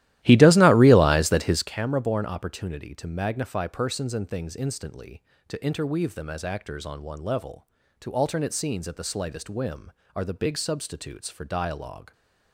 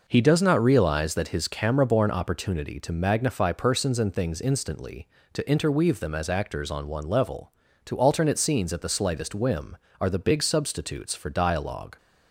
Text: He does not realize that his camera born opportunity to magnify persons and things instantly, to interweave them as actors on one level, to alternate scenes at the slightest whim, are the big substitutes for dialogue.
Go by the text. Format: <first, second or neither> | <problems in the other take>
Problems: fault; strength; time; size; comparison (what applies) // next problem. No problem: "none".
second | starts louder than the rest; strong; until 1.7 s; 14.5 dB